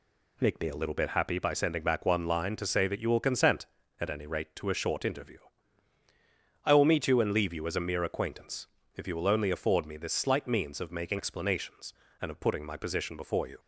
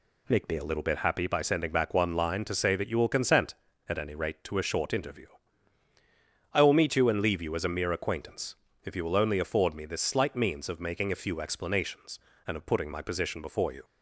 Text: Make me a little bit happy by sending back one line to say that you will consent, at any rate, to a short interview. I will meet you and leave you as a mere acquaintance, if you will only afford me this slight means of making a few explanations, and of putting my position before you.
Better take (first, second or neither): second